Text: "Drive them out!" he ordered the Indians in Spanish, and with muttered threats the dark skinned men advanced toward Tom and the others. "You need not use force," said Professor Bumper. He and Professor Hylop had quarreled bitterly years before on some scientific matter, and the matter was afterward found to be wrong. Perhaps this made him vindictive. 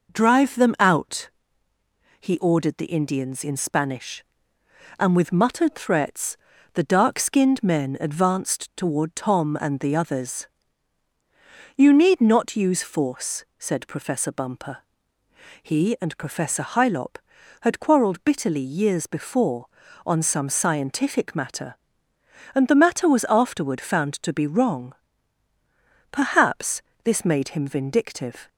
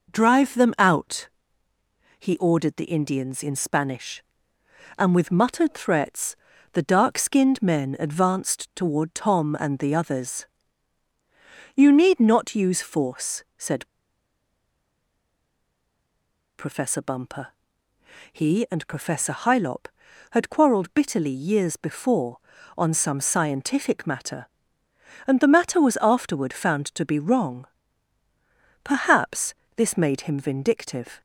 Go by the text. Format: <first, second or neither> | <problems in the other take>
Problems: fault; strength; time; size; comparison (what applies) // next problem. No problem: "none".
first | pauses between "threats" and "the"; slight; at 6.3 s; 0.36 s long; slight in the first // pauses between "said" and "Professor"; strong; at 13.8 s; 2.7 s long // pauses between "Perhaps" and "this"; slight; at 29.5 s; 0.24 s long; slight in the first